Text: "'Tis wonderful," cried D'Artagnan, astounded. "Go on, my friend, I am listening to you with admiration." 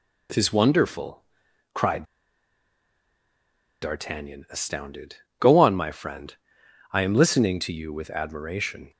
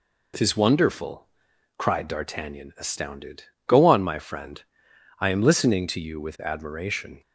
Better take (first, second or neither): second